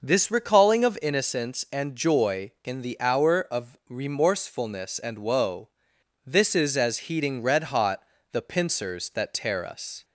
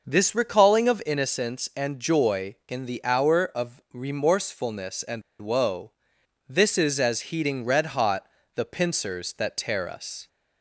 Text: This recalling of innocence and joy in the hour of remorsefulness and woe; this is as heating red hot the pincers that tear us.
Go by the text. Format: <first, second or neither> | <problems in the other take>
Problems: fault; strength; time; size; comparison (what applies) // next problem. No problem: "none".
first | pauses between "and" and "woe"; slight; at 5.2 s; 0.19 s long // pauses between "hot" and "the"; slight; at 8.2 s; 0.26 s long; slight in the first